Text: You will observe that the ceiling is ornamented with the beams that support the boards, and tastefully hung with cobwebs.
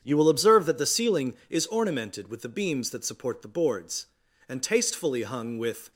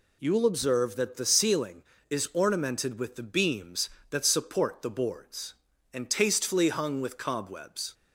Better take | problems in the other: second | starts louder than the rest; strong; until 1.0 s; 8 dB // stops before "cobwebs"; at 5.9 s

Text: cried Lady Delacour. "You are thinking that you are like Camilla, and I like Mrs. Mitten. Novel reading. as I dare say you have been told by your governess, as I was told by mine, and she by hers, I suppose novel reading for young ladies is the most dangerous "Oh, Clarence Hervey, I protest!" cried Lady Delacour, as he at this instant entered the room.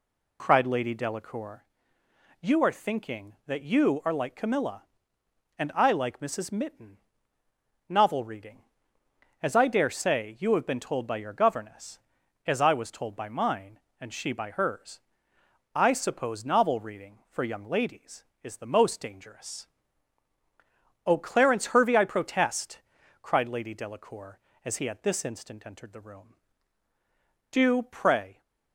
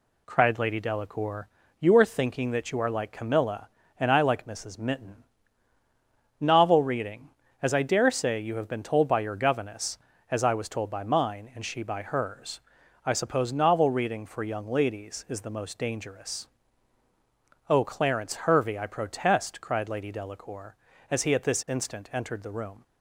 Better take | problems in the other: second | pauses between "dangerous" and "Oh"; strong; at 19.6 s; 1.3 s long; also in the second // goes on to say "Do pray"; noticeable; from 27.5 s on; 0.90 s long

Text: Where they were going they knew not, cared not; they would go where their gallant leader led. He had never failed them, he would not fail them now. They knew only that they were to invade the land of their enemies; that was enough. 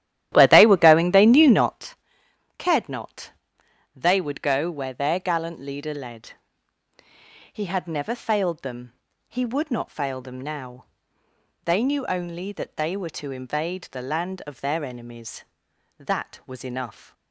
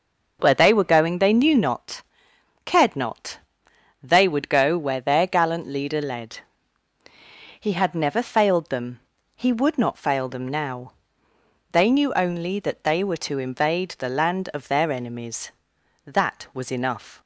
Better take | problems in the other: second | starts louder than the rest; strong; until 1.8 s; 12.5 dB

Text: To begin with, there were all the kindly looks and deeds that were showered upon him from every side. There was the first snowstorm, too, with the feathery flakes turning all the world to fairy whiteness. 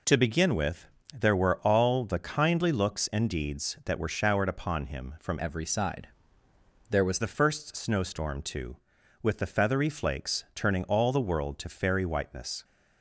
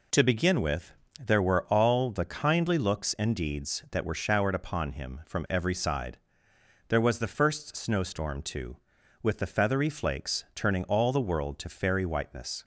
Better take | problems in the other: second | changes voice from "every" to "was"; from 5.3 to 7.1 s; 1.8 s long

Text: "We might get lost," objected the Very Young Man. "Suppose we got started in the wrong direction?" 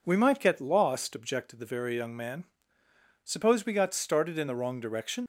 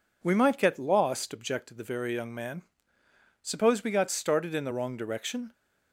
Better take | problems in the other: second | leaves "direction" unfinished; at 5.2 s; 95 ms

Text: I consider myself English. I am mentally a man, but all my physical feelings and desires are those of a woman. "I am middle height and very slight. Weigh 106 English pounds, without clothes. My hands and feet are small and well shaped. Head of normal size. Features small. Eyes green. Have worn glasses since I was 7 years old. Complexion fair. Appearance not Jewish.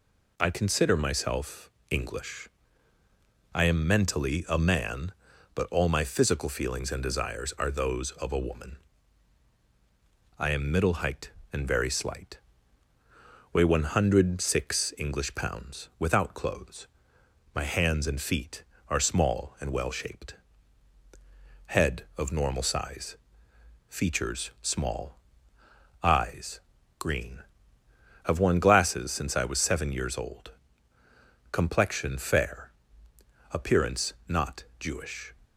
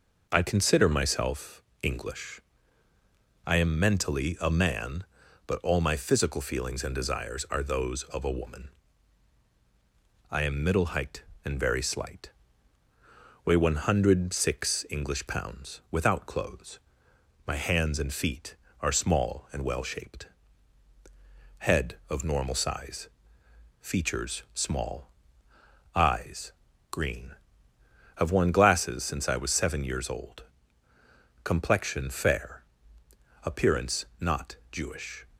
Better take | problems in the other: first | starts louder than the rest; noticeable; until 1.4 s; 5 dB // pauses between "myself" and "English"; slight; at 1.6 s; 0.20 s long; slight in the first // pauses between "Eyes" and "green"; at 26.5 s; 0.40 s long; also in the first // pauses between "not" and "Jewish"; slight; at 34.5 s; 0.16 s long; slight in the first

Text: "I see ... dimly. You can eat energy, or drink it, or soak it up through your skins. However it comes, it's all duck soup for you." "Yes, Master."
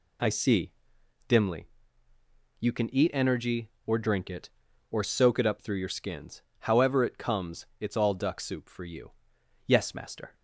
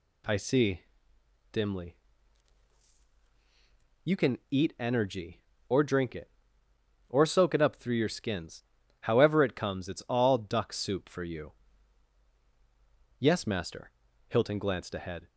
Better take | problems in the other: first | goes on to say "Hilton glanced ahead"; noticeable; from 14.2 s on; 0.98 s long

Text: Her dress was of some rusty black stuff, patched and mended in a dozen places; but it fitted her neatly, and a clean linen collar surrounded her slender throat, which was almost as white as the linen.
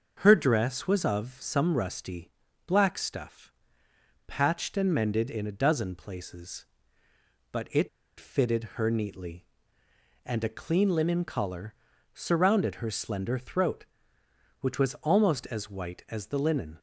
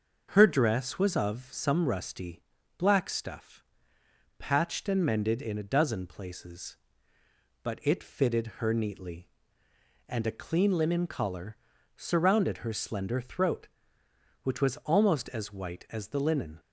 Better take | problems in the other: second | starts louder than the rest; noticeable; until 1.2 s; 6 dB; also in the second // pauses between "rusty" and "black"; slight; at 2.3 s; 0.34 s long; slight in the second // pauses between "it" and "fitted"; slight; at 7.8 s; 0.31 s long // pauses between "fitted" and "her"; slight; at 8.6 s; 0.16 s long; slight in the second // pauses between "collar" and "surrounded"; at 11.7 s; 0.40 s long; also in the second

